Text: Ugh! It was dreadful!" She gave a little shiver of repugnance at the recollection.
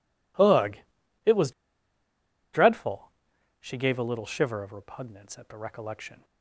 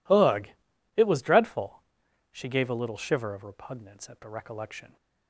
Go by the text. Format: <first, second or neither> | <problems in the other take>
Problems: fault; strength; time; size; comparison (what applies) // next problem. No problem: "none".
second | pauses between "was" and "dreadful"; at 1.5 s; 1.0 s long